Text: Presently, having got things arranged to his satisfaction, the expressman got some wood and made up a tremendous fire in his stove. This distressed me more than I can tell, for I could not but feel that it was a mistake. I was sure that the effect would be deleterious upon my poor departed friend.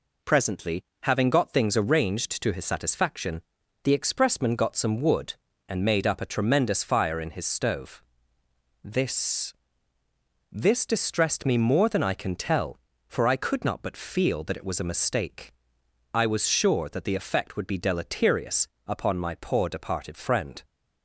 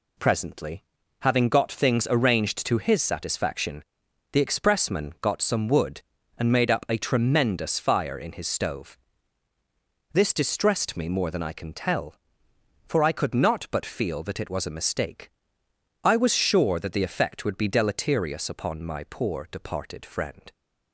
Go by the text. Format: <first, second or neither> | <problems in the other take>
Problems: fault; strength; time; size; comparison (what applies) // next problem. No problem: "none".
second | says "This" twice; at 10.5 s // pauses between "deleterious" and "upon"; slight; at 18.6 s; 0.18 s long